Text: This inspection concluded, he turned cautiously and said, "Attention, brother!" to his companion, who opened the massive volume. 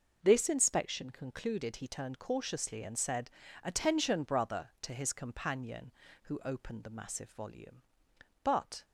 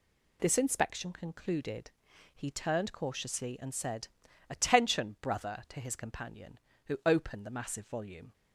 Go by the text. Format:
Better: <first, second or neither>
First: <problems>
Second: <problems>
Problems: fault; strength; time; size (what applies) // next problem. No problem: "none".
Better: second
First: goes on to say "But"; slight; from 8.4 s on; 0.42 s long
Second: none